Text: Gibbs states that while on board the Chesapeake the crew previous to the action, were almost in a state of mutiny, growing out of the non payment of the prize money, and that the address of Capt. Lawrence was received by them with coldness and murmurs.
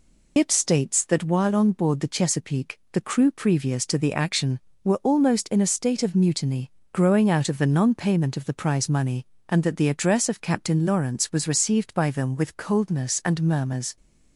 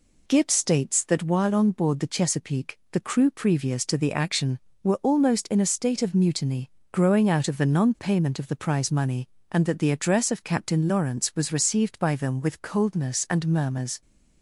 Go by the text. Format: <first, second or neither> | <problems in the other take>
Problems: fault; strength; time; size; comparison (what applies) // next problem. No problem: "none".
second | loses the start of "Gibbs"; at 0.3 s; 75 ms